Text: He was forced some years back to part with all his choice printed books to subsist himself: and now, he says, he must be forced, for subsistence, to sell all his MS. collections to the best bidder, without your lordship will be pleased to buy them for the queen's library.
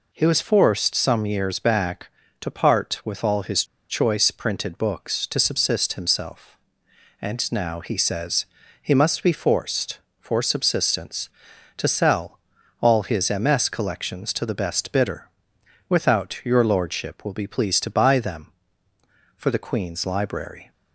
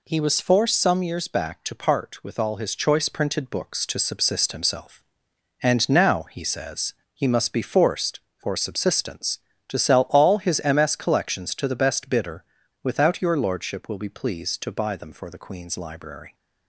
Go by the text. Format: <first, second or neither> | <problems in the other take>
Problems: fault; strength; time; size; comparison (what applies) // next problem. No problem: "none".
second | pauses between "his" and "choice"; slight; at 3.6 s; 0.24 s long // pauses between "sell" and "all"; at 12.3 s; 0.44 s long